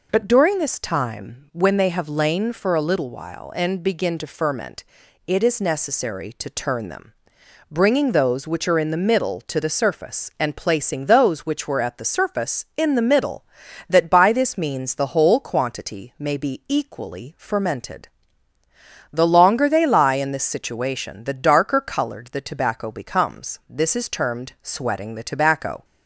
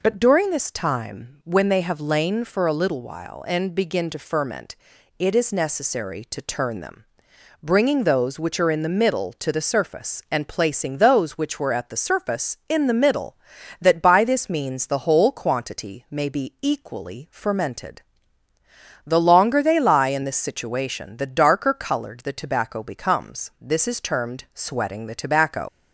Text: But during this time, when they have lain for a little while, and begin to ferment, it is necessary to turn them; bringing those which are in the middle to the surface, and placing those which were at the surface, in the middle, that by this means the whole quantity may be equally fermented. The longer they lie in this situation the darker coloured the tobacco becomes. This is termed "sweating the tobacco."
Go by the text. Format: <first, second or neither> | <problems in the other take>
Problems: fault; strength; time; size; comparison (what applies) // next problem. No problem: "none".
first | leaves "tobacco" unfinished; at 25.6 s; 70 ms